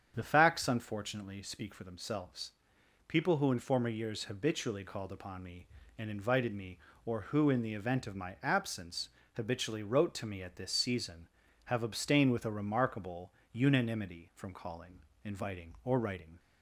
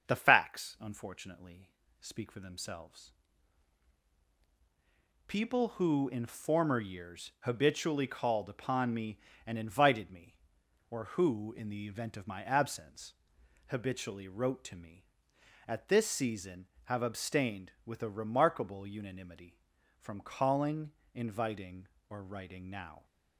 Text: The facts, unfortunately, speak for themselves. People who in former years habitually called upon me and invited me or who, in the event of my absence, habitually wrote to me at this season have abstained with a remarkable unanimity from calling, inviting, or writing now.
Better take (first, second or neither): second